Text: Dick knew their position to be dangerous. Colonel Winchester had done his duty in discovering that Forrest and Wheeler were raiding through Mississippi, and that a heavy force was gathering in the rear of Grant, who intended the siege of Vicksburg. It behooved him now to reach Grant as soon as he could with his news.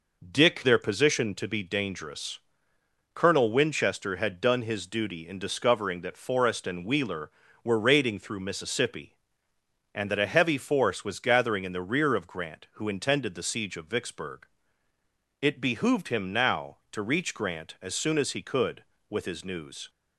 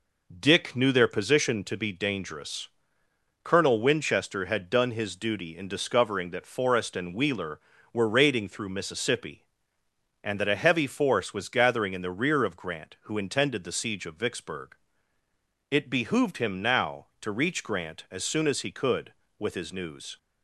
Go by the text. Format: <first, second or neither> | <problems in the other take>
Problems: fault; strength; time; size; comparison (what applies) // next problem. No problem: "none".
second | skips "knew"; at 0.6 s